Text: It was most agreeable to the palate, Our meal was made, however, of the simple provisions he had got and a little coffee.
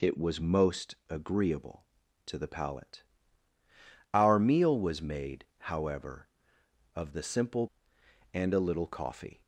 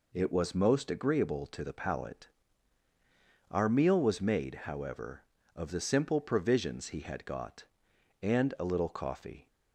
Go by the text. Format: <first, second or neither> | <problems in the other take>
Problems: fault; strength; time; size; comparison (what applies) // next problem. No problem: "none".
second | pauses between "most" and "agreeable"; slight; at 0.9 s; 0.16 s long // skips "provisions he had got"; at 7.9 s